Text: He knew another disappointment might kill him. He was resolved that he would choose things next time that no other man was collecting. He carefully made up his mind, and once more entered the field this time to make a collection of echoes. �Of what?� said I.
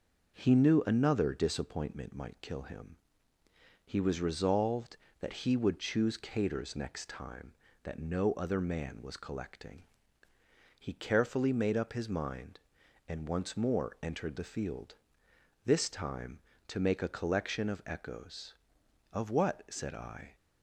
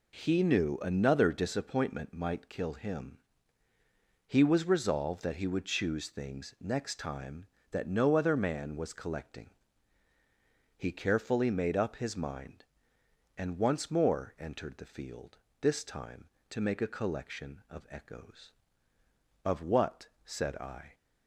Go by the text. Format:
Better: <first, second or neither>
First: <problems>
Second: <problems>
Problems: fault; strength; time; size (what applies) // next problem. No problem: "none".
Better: second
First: says "caters" for "things"; at 6.1 s // pauses between "field" and "this"; noticeable; at 14.9 s; 0.70 s long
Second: pauses between "field" and "this"; slight; at 15.3 s; 0.26 s long